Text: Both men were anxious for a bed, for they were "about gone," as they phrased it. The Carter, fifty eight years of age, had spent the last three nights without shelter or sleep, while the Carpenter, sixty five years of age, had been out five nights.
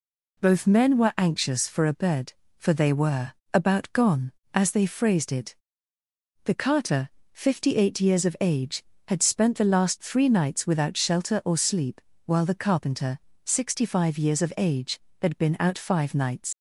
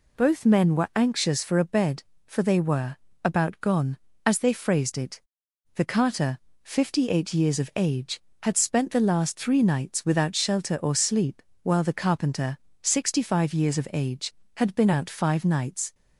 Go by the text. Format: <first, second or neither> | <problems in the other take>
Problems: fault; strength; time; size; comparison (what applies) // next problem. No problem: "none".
second | pauses between "were" and "about"; slight; at 3.3 s; 0.24 s long; slight in the second // leaves "nights" unfinished; at 16.5 s; 85 ms